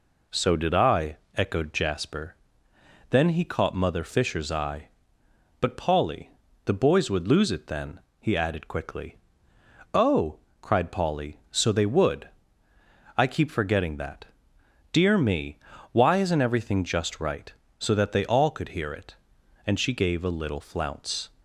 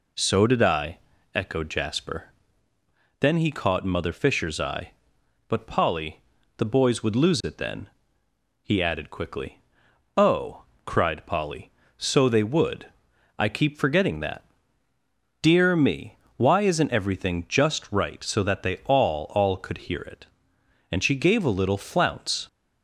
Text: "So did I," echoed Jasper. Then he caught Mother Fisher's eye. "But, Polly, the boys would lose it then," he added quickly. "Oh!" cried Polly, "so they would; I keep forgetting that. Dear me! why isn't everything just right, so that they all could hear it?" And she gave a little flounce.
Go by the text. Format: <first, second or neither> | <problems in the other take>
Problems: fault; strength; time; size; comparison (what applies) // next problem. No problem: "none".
first | says "all" twice; at 19.3 s